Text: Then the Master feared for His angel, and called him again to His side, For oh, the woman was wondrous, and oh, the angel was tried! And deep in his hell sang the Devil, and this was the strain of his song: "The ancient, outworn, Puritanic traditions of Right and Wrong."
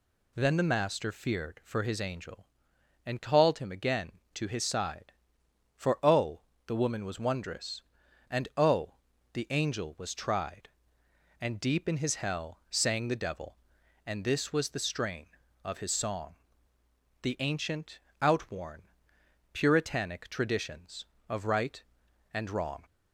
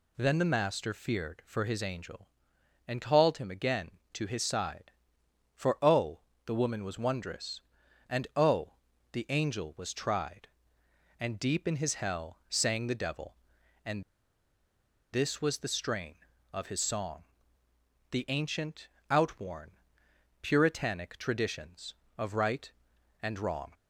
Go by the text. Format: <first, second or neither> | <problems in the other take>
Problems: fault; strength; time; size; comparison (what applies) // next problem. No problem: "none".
first | pauses between "and" and "this"; at 14.0 s; 1.1 s long